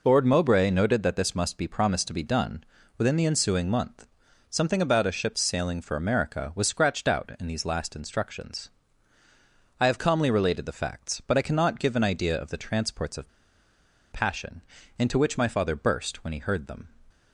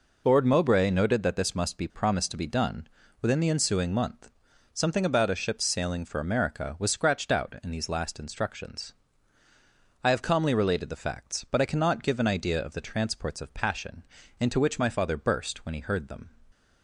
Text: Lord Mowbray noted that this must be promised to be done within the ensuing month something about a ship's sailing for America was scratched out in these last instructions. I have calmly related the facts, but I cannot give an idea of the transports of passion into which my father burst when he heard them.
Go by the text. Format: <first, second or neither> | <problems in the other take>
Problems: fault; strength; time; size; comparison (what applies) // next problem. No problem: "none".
second | pauses between "done" and "within"; slight; at 2.6 s; 0.34 s long; slight in the second // pauses between "month" and "something"; at 4.0 s; 0.44 s long; also in the second // pauses between "of" and "passion"; noticeable; at 13.2 s; 0.82 s long // pauses between "passion" and "into"; slight; at 14.6 s; 0.36 s long; slight in the second